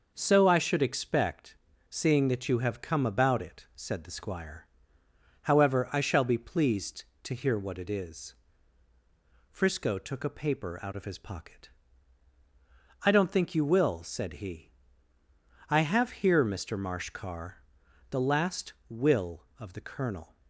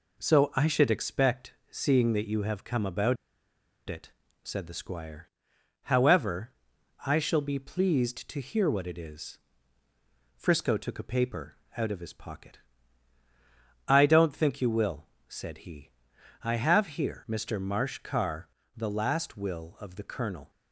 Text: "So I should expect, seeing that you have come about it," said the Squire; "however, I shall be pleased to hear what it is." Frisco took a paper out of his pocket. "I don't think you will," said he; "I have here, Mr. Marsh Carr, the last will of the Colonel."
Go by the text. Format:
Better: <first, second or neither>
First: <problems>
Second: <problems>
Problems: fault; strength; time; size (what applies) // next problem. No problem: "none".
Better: first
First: none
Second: pauses between "about" and "it"; noticeable; at 3.1 s; 0.73 s long // pauses between "paper" and "out"; slight; at 11.5 s; 0.22 s long